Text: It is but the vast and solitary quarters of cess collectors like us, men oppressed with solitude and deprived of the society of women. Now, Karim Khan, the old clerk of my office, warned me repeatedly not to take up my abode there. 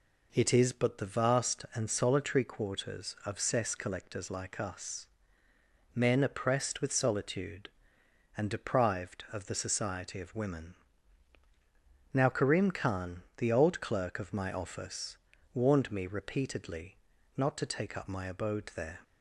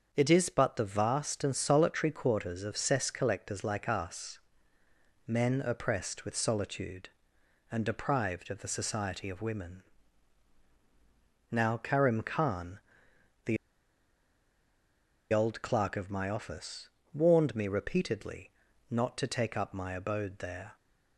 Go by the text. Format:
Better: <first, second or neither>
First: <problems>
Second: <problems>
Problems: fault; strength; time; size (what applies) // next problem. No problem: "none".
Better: first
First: pauses between "repeatedly" and "not"; at 16.9 s; 0.40 s long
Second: starts louder than the rest; until 1.1 s; 6.5 dB // pauses between "the" and "old"; strong; at 13.5 s; 1.7 s long // pauses between "repeatedly" and "not"; at 18.4 s; 0.40 s long